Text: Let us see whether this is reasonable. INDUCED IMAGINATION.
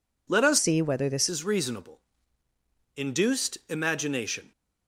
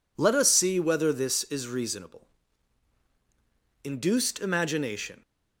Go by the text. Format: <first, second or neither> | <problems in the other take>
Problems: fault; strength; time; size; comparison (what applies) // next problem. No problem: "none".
second | changes voice from "see" to "this"; from 0.5 to 1.2 s; 0.7 s long